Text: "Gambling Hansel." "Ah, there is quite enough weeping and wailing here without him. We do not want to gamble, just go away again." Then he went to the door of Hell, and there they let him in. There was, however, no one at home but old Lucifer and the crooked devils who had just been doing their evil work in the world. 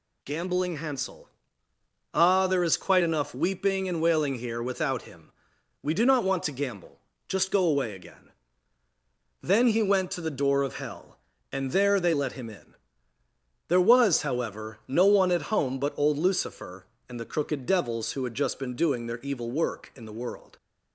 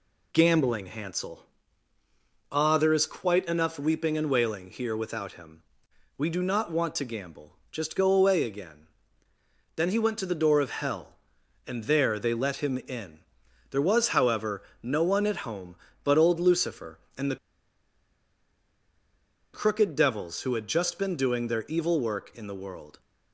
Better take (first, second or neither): first